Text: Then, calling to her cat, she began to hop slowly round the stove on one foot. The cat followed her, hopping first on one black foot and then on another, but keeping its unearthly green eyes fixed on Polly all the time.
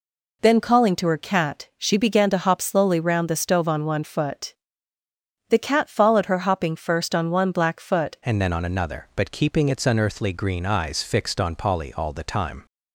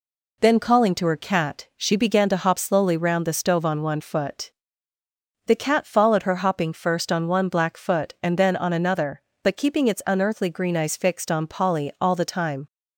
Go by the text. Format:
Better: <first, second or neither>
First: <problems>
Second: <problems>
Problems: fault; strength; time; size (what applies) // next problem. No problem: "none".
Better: second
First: changes voice at "and"; from 8.2 s on; 4.4 s long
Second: none